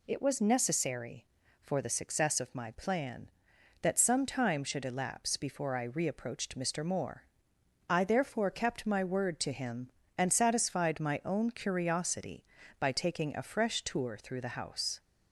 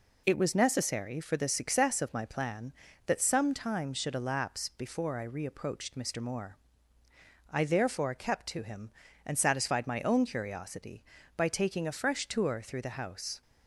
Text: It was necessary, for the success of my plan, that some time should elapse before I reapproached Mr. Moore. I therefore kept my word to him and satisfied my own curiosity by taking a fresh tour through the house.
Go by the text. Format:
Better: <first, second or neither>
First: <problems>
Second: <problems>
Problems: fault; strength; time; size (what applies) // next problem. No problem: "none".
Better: first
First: none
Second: skips "my word"; at 8.4 s